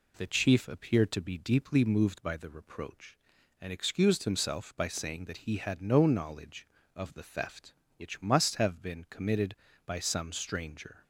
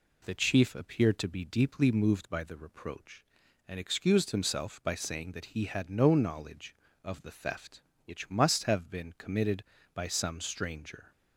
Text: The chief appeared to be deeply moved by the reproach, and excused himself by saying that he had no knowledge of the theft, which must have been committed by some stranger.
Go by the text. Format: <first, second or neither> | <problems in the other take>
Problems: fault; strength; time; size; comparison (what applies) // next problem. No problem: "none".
neither | none